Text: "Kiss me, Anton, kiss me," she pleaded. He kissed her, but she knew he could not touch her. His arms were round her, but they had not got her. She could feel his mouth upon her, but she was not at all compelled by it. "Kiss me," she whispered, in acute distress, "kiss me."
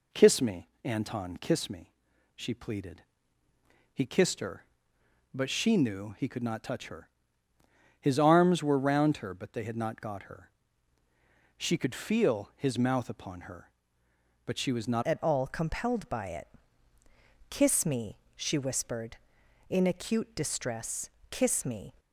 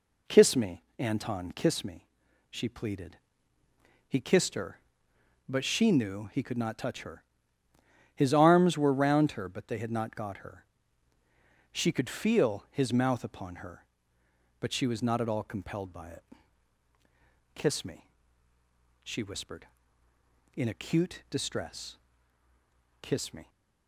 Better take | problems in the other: second | changes voice at "at"; from 15.0 s on; 6.9 s long

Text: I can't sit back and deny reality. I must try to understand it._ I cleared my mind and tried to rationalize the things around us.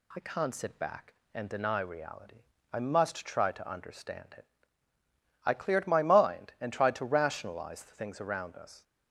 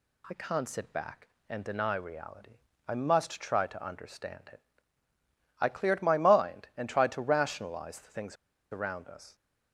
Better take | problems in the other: first | pauses between "things" and "around"; slight; at 8.3 s; 0.36 s long

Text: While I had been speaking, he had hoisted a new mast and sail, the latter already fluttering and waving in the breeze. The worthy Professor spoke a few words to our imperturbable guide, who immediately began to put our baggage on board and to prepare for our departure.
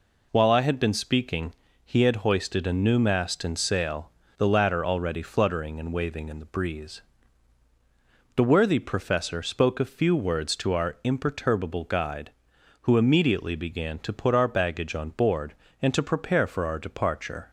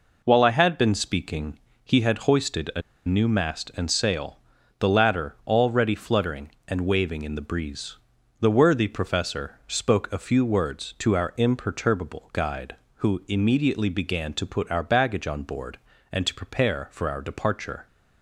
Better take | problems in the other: first | pauses between "a" and "new"; slight; at 2.8 s; 0.25 s long

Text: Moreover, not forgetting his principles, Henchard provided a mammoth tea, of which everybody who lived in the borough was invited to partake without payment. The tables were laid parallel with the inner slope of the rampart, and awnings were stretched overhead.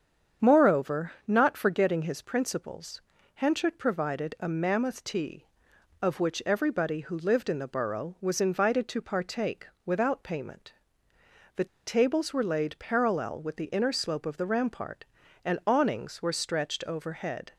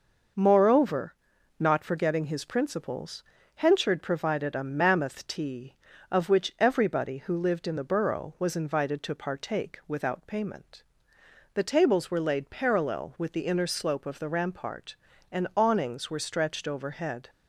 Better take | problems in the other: second | starts louder than the rest; strong; until 1.5 s; 7.5 dB // pauses between "partake" and "without"; slight; at 9.6 s; 0.18 s long // pauses between "The" and "tables"; slight; at 11.6 s; 0.21 s long

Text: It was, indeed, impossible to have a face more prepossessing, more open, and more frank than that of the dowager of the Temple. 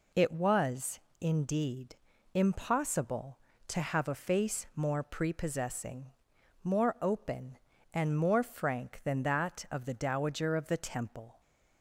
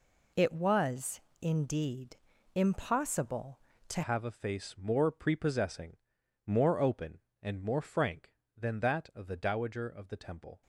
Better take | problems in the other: first | changes voice at "have"; from 4.0 s on; 6.6 s long

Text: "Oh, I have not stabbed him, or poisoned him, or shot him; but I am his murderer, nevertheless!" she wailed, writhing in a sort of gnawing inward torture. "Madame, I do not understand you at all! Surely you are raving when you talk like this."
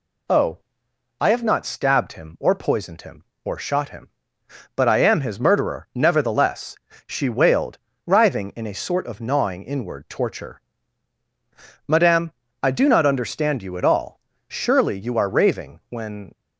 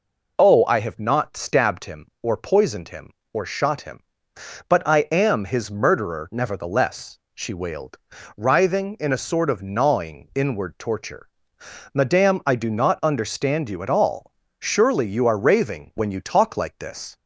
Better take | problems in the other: second | stops before "you talk like this"; at 16.3 s

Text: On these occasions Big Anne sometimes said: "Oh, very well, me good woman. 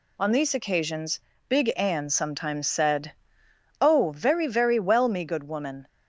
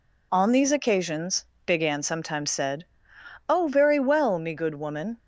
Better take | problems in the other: second | pauses between "occasions" and "Big"; slight; at 1.1 s; 0.30 s long; slight in the second // says "very" twice; at 4.4 s

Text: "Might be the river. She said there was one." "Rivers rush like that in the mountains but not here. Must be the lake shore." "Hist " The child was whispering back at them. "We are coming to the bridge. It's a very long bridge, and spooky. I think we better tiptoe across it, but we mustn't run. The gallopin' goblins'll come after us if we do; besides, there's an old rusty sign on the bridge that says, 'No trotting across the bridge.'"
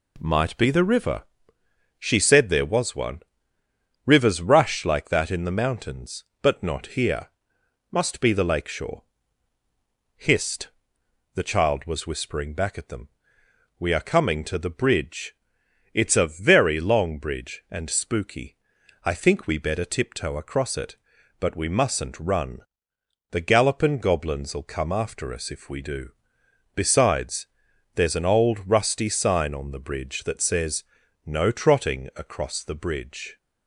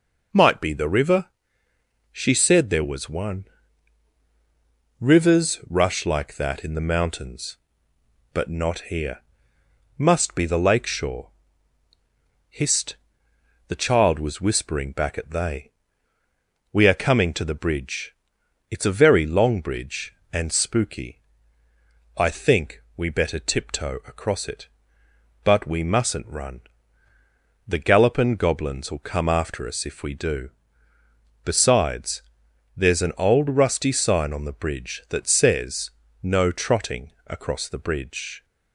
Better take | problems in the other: first | says "they" for "them"; at 15.3 s // pauses between "trotting" and "across"; slight; at 37.1 s; 0.16 s long

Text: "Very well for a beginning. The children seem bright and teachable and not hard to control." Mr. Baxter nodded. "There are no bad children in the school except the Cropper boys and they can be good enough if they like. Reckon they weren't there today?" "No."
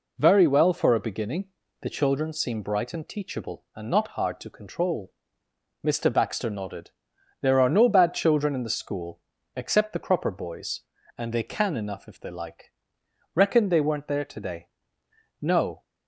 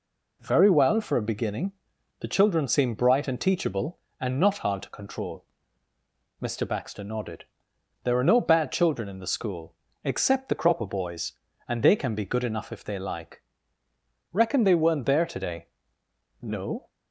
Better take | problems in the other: second | pauses between "school" and "except"; slight; at 9.2 s; 0.34 s long; slight in the second // skips "be good"; at 11.7 s

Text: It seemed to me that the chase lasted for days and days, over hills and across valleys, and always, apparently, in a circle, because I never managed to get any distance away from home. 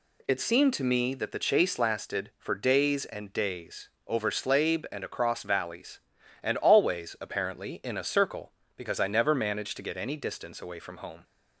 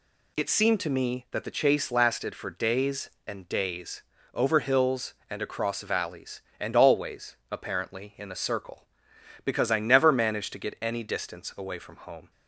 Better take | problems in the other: second | says "slabe" for "hills"; at 4.2 s

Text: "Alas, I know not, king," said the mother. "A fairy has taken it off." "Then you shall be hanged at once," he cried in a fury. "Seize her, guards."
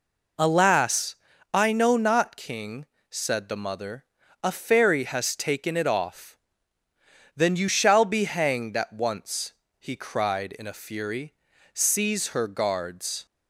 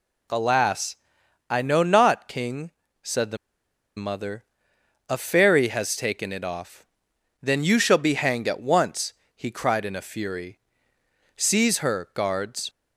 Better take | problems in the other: first | pauses between "the" and "mother"; noticeable; at 3.3 s; 0.60 s long

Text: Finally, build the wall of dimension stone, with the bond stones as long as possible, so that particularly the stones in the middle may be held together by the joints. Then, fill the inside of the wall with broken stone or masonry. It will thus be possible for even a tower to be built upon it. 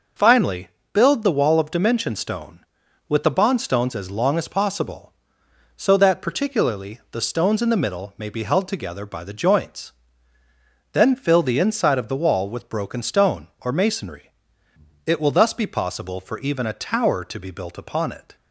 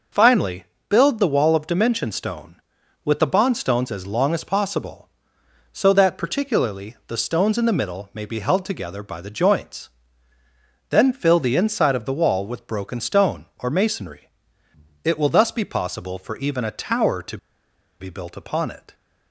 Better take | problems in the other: first | pauses between "to" and "be"; noticeable; at 17.3 s; 0.62 s long

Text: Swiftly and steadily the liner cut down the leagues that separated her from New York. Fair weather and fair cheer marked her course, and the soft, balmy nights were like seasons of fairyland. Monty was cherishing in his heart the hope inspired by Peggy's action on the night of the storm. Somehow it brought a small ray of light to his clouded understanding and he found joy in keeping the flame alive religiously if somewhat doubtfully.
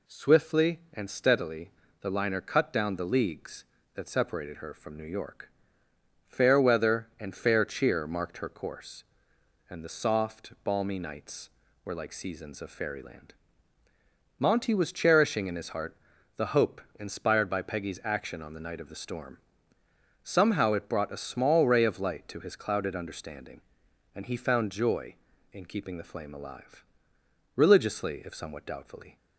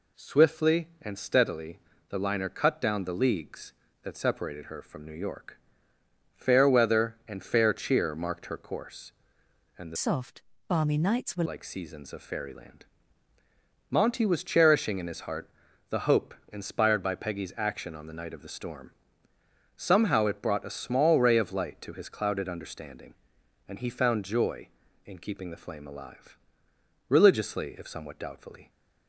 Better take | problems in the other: first | pauses between "steadily" and "the"; slight; at 1.8 s; 0.30 s long; slight in the first // changes voice from "soft" to "were"; from 9.9 to 11.4 s; 1.5 s long // pauses between "heart" and "the"; at 15.4 s; 0.42 s long; also in the first // pauses between "hope" and "inspired"; slight; at 16.3 s; 0.18 s long; slight in the first // pauses between "alive" and "religiously"; noticeable; at 26.3 s; 0.72 s long; noticeable in the first

